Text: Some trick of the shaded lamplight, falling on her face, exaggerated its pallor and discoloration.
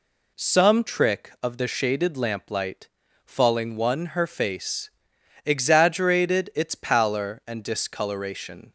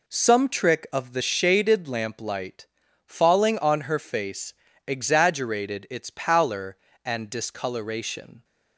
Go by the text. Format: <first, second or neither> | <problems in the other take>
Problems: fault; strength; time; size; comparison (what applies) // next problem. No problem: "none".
second | says "one" for "on"; at 3.7 s